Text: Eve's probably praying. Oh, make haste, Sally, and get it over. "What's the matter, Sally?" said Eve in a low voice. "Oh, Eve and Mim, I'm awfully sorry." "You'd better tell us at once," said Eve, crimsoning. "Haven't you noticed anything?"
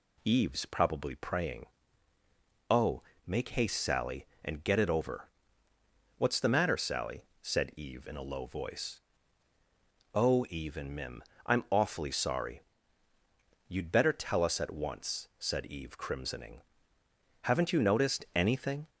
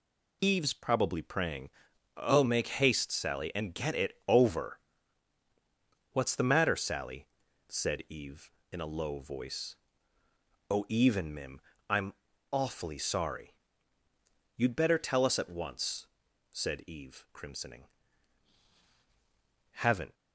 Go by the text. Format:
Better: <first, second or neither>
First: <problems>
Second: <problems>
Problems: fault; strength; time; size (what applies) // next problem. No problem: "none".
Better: first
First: none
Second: pauses between "I'm" and "awfully"; at 12.1 s; 0.38 s long // stops before "you noticed anything"; at 20.1 s